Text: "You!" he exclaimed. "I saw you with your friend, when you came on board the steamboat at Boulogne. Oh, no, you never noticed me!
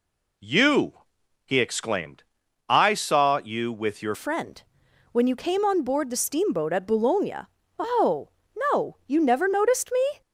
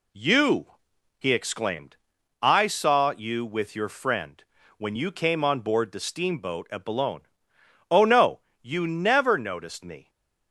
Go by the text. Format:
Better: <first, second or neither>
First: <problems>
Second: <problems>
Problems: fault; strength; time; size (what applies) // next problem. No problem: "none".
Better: second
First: changes voice at "friend"; from 4.1 s on; 6.1 s long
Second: none